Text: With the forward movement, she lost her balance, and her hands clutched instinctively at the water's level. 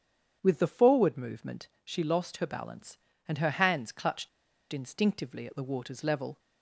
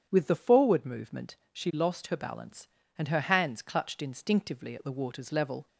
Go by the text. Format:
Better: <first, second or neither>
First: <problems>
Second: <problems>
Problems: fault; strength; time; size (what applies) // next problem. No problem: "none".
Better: second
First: starts louder than the rest; strong; until 1.4 s; 8.5 dB // pauses between "clutched" and "instinctively"; at 4.2 s; 0.43 s long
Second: starts louder than the rest; strong; until 1.1 s; 8.5 dB